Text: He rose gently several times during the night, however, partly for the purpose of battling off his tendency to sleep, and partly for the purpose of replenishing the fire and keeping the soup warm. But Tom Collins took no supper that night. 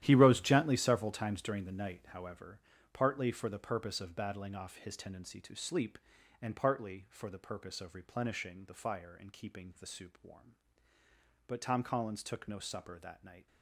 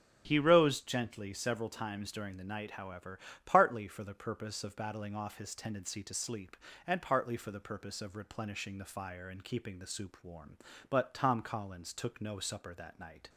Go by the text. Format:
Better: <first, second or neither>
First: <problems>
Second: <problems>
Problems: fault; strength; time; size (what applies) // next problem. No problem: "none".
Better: second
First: gets quieter; strong; throughout; 12.5 dB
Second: none